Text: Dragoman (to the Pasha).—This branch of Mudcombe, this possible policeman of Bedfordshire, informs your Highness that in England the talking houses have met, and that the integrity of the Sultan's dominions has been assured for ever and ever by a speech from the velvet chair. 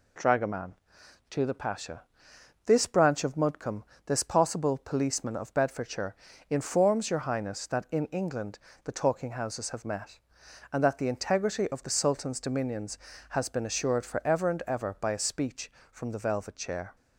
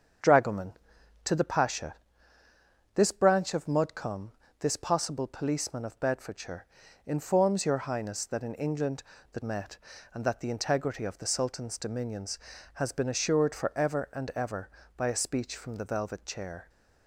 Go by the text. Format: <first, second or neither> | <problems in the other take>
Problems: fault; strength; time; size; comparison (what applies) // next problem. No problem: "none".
first | starts louder than the rest; strong; until 1.7 s; 7.5 dB // pauses between "England" and "the"; slight; at 9.0 s; 0.30 s long; slight in the first // skips "talking houses have"; at 9.4 s